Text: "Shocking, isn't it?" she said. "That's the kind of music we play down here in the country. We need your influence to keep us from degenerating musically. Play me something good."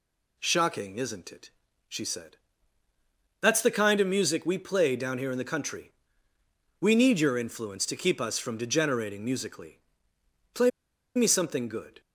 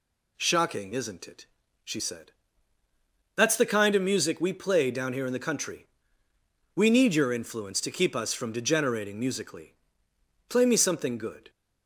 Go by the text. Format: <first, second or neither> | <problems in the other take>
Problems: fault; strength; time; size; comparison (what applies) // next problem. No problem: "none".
second | pauses between "Play" and "me"; noticeable; at 10.6 s; 0.46 s long